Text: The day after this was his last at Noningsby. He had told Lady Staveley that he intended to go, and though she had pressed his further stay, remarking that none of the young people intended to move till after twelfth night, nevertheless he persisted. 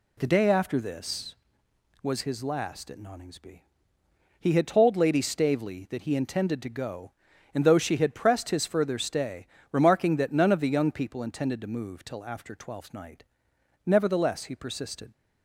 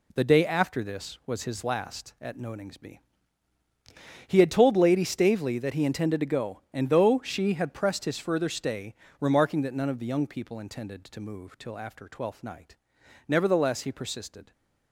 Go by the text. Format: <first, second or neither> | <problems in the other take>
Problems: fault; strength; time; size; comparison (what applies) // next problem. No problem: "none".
first | gets quieter; strong; throughout; 8 dB